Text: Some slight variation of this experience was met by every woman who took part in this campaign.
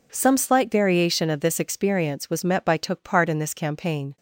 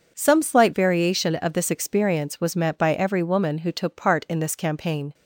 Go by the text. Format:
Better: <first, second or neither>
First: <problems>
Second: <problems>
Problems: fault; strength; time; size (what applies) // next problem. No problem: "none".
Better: second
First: skips "every woman who"; at 2.7 s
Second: none